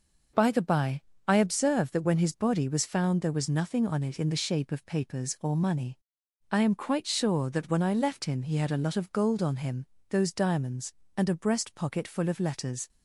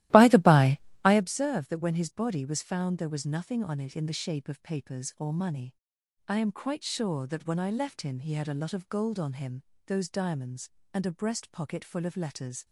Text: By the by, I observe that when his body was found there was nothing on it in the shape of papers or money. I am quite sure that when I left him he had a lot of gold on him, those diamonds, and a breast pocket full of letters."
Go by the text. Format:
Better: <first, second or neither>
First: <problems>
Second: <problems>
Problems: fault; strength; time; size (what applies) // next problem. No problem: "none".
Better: first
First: none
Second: starts louder than the rest; strong; until 1.3 s; 16 dB